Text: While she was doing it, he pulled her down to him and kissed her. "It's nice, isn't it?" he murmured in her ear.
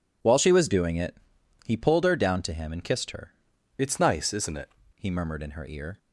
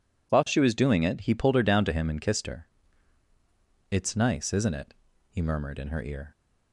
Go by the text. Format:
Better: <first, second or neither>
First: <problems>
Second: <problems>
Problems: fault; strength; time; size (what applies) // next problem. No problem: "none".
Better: second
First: changes voice from "It's" to "it"; from 3.7 to 4.6 s; 0.9 s long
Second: none